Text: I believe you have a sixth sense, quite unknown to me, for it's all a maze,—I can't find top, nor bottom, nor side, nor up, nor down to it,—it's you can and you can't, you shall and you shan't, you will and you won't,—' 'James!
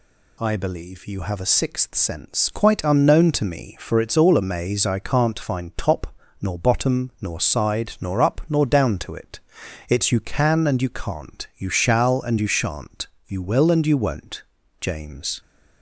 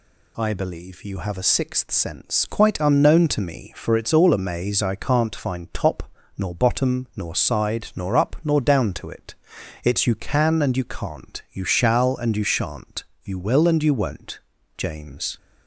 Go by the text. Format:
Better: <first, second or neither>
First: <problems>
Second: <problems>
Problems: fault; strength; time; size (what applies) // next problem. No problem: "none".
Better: neither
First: none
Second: none